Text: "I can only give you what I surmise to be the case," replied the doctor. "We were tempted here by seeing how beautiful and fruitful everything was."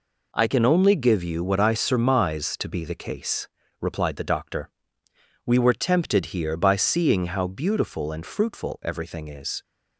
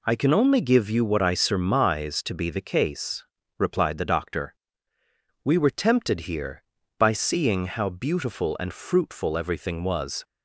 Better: second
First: says "is" for "was"; at 9.2 s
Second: none

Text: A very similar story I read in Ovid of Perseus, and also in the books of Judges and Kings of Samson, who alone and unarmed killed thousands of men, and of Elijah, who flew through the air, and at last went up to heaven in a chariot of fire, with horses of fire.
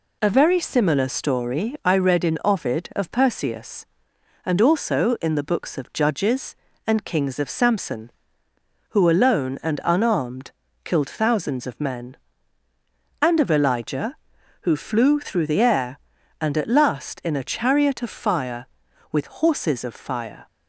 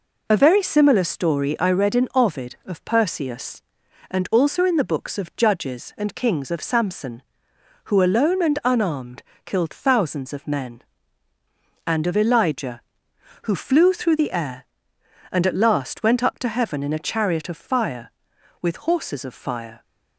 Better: second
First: pauses between "unarmed" and "killed"; slight; at 10.5 s; 0.34 s long // skips "went up to heaven"; at 17.2 s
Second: pauses between "unarmed" and "killed"; slight; at 9.2 s; 0.22 s long

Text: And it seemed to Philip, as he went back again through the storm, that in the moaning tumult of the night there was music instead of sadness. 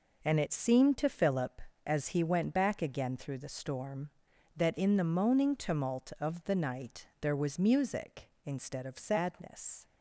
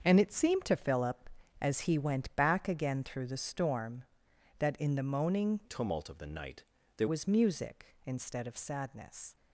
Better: first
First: none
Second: starts louder than the rest; until 1.0 s; 7 dB // changes voice from "tumult" to "there"; from 5.6 to 7.0 s; 1.4 s long // pauses between "night" and "there"; slight; at 6.6 s; 0.34 s long

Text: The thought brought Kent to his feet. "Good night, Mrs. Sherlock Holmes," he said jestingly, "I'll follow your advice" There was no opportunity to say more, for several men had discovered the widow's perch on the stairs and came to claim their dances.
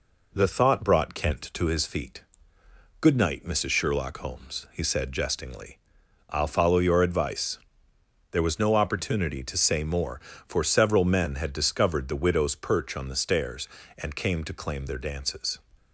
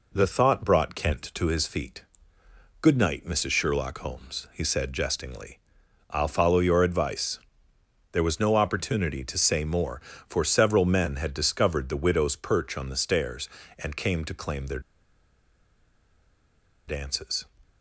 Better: first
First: pauses between "advice" and "There"; noticeable; at 7.5 s; 0.72 s long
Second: pauses between "advice" and "There"; noticeable; at 7.3 s; 0.72 s long // pauses between "their" and "dances"; strong; at 14.8 s; 2.0 s long

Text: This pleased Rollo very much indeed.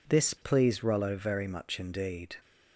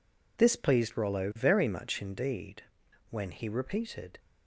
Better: first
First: none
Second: goes on to say "When he repeated"; noticeable; from 3.0 s on; 1.1 s long

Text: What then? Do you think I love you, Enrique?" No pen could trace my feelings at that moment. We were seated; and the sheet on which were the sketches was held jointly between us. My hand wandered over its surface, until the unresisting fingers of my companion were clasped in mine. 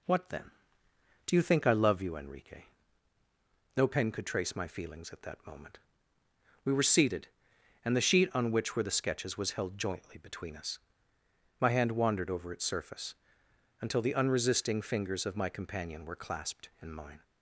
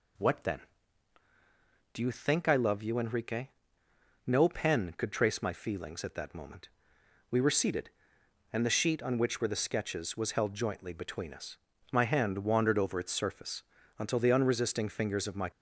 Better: first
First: none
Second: stops before "companion were clasped in mine"; at 15.5 s

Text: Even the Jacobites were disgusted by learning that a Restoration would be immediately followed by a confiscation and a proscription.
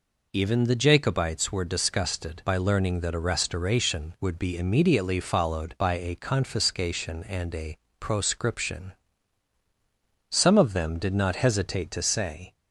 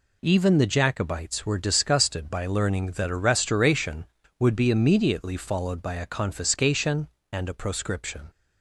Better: second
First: pauses between "a" and "proscription"; slight; at 7.7 s; 0.22 s long // goes on to say "Some of them did not hesitate to say"; strong; from 10.3 s on; 2.2 s long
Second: none

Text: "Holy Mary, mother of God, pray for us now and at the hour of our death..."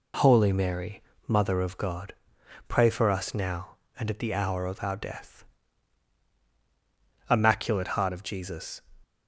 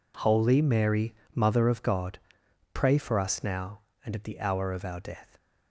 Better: second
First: goes on to say "Immaculate heart of Jesus"; from 7.2 s on; 1.5 s long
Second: none

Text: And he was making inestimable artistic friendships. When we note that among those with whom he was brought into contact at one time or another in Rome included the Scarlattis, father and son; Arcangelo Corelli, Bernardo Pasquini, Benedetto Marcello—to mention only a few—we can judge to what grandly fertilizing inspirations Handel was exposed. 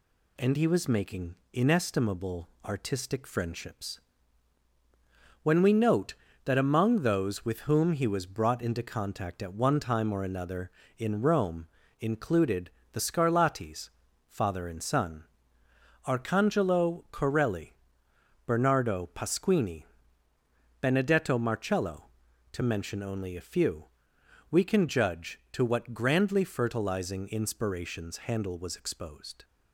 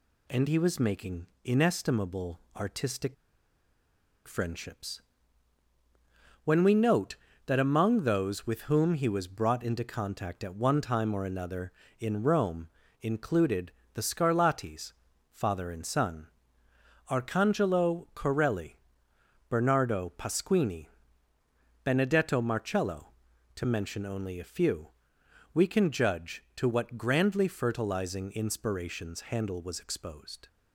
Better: first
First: pauses between "making" and "inestimable"; slight; at 1.3 s; 0.16 s long // pauses between "inestimable" and "artistic"; slight; at 2.4 s; 0.16 s long // pauses between "Rome" and "included"; slight; at 11.6 s; 0.34 s long // pauses between "included" and "the"; slight; at 12.6 s; 0.22 s long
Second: pauses between "making" and "inestimable"; slight; at 1.2 s; 0.16 s long // pauses between "inestimable" and "artistic"; slight; at 2.3 s; 0.16 s long // pauses between "artistic" and "friendships"; at 3.1 s; 1.1 s long // pauses between "Rome" and "included"; slight; at 12.6 s; 0.34 s long // pauses between "included" and "the"; slight; at 13.7 s; 0.22 s long

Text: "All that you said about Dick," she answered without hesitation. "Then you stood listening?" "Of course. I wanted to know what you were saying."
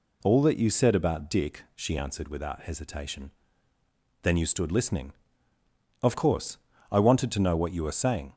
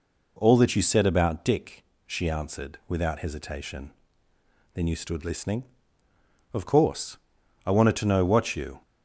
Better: first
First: none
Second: stops before "were saying"; at 8.8 s

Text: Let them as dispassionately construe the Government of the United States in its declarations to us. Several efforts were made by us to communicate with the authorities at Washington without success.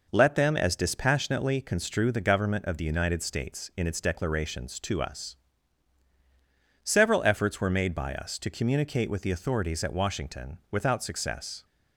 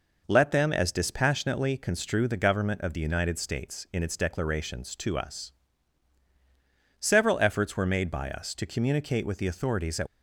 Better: first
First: none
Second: stops before "Washington without success"; at 10.0 s

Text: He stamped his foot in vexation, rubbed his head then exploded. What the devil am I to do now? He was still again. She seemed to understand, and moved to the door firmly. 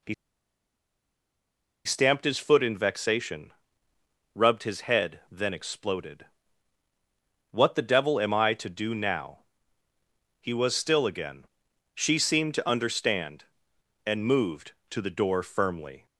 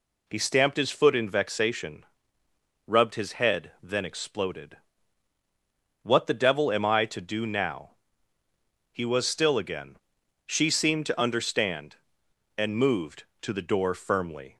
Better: second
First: pauses between "He" and "stamped"; strong; at 0.1 s; 1.7 s long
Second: none

